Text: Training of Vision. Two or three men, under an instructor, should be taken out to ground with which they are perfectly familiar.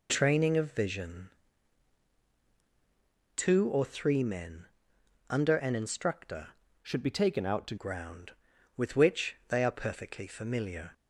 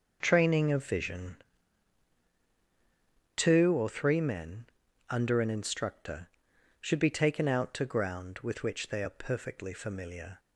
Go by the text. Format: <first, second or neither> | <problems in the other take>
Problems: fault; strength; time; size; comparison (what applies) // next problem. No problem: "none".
second | changes voice from "should" to "to"; from 6.8 to 7.7 s; 0.9 s long